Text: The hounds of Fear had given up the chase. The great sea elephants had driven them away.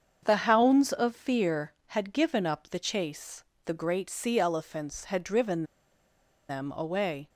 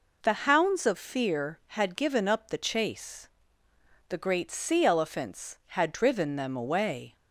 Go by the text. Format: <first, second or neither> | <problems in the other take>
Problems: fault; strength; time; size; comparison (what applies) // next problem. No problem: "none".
second | starts louder than the rest; strong; until 1.2 s; 7 dB // pauses between "driven" and "them"; noticeable; at 5.6 s; 0.85 s long